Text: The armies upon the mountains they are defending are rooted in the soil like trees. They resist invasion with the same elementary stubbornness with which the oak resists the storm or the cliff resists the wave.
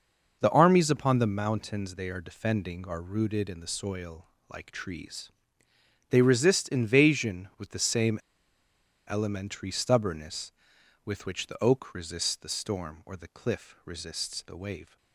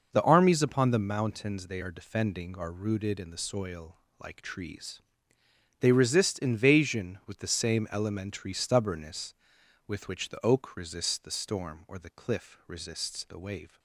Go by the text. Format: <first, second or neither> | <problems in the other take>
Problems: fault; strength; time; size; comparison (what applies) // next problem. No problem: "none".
second | pauses between "soil" and "like"; slight; at 4.2 s; 0.26 s long; slight in the second // pauses between "same" and "elementary"; noticeable; at 8.1 s; 0.90 s long